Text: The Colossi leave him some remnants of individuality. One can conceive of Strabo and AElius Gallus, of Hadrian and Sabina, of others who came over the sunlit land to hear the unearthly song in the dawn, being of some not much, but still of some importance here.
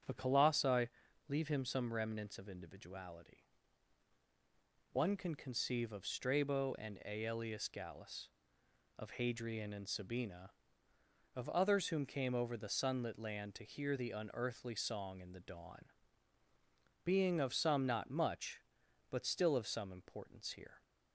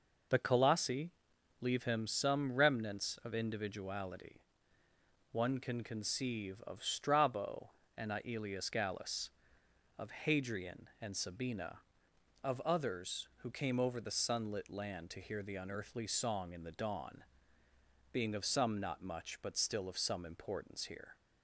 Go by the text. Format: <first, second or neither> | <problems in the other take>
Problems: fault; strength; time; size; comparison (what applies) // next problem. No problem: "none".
second | starts louder than the rest; strong; until 1.4 s; 7.5 dB // pauses between "Colossi" and "leave"; at 0.8 s; 0.40 s long; noticeable in the second // says "whom" for "who"; at 11.8 s